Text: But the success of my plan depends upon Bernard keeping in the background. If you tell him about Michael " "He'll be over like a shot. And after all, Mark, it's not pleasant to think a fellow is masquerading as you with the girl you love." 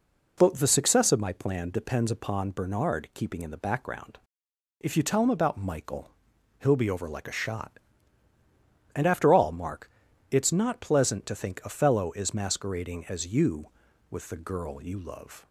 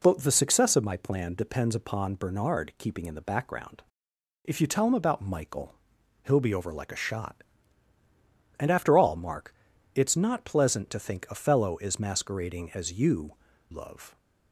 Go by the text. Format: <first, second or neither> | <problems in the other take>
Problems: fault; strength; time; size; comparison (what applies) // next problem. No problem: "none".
first | skips "with the girl you"; at 13.5 s